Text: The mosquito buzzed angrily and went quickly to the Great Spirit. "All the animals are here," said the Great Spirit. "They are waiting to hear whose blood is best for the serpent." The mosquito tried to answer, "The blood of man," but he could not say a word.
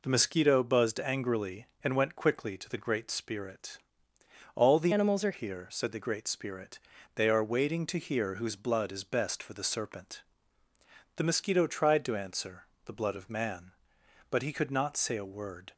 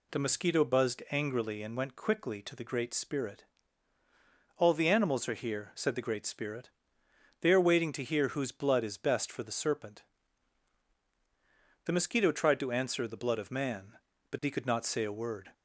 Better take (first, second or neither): second